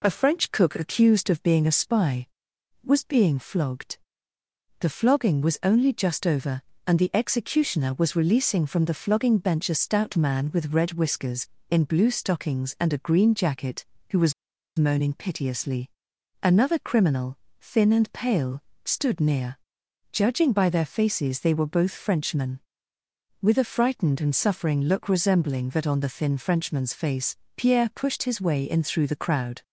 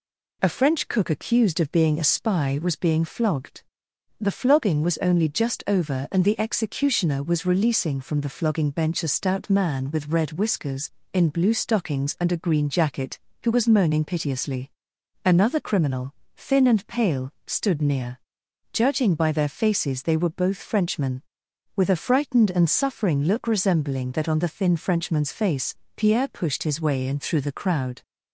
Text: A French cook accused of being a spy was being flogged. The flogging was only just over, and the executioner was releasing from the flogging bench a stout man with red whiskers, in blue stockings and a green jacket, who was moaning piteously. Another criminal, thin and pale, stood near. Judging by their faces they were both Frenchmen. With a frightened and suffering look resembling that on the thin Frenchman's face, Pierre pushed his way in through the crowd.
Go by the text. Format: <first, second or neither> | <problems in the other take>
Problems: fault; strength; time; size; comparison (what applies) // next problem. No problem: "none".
second | pauses between "was" and "moaning"; at 14.3 s; 0.45 s long